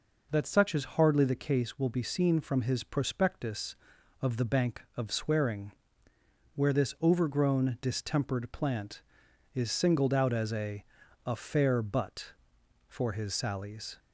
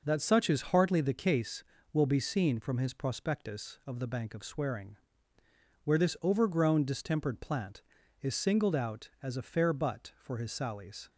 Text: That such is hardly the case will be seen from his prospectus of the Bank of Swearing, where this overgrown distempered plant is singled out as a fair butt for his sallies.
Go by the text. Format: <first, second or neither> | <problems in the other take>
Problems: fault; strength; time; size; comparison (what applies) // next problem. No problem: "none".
second | says "a" twice; at 11.2 s